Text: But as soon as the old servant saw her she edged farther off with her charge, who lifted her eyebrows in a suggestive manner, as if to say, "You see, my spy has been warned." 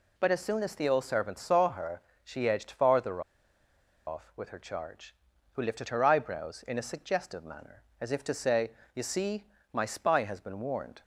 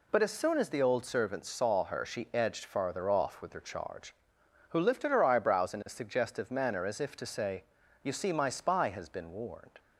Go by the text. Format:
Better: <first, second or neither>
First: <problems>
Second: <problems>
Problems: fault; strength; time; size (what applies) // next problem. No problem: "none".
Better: second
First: pauses between "her" and "she"; slight; at 1.9 s; 0.24 s long // pauses between "farther" and "off"; noticeable; at 3.1 s; 0.86 s long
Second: none